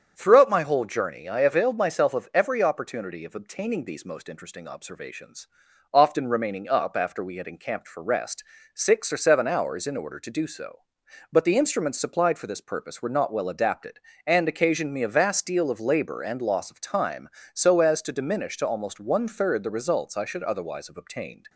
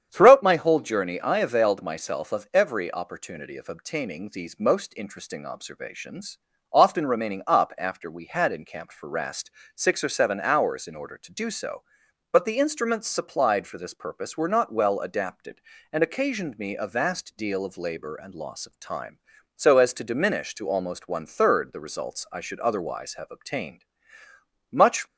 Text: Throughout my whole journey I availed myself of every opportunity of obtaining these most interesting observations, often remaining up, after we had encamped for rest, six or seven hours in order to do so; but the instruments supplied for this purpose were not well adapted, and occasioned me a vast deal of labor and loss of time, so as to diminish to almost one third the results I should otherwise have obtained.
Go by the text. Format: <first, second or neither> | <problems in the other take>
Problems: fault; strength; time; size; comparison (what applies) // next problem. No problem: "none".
first | starts louder than the rest; strong; until 1.1 s; 8.5 dB; strong in the first // goes on to say "Much"; slight; from 24.7 s on; 0.34 s long